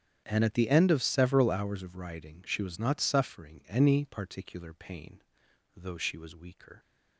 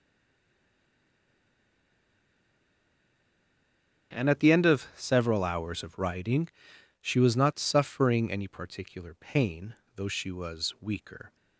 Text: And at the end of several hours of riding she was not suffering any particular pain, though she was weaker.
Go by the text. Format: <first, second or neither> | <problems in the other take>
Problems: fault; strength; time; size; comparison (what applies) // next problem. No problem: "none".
first | stays silent before the first word; strong; until 4.1 s; 4.1 s long // starts louder than the rest; strong; until 5.1 s; 9 dB; strong in the first // pauses between "riding" and "she"; noticeable; at 6.4 s; 0.56 s long